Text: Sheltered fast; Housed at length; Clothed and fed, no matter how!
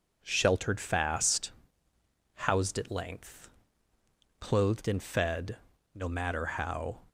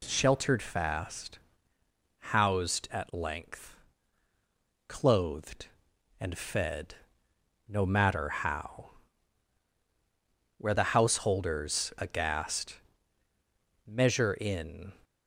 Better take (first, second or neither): first